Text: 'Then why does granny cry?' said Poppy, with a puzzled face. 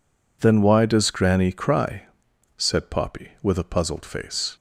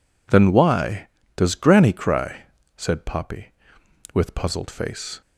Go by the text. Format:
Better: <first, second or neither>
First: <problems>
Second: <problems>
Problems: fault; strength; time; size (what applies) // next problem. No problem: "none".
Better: first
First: none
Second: skips "a"; at 4.3 s